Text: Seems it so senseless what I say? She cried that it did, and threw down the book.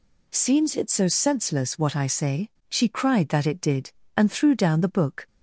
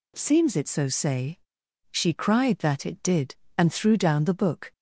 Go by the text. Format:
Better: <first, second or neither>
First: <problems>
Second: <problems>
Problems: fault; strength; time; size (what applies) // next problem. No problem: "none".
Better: first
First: none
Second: skips "senseless what I"; at 0.8 s